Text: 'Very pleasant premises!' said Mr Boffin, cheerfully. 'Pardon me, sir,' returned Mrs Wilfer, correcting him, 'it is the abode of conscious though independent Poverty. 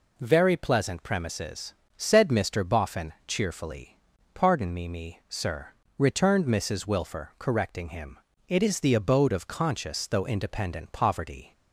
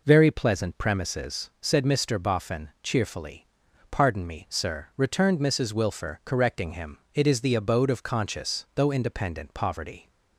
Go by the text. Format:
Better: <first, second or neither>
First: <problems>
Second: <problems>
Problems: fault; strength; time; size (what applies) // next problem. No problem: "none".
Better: second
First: says "me" twice; at 4.8 s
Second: none